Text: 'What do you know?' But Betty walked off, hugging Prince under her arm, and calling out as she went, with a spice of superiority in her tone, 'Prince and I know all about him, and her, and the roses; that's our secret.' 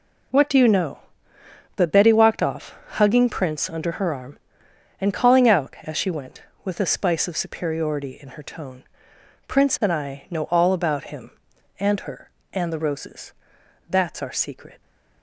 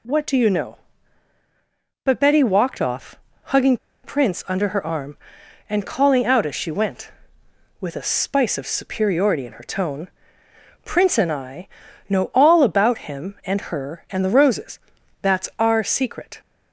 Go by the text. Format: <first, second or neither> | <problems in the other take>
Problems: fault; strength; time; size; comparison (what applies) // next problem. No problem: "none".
first | pauses between "hugging" and "Prince"; slight; at 3.7 s; 0.27 s long // pauses between "I" and "know"; at 11.6 s; 0.40 s long